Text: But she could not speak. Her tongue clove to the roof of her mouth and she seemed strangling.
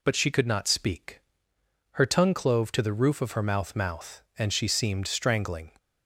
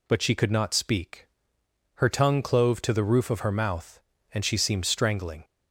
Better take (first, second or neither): second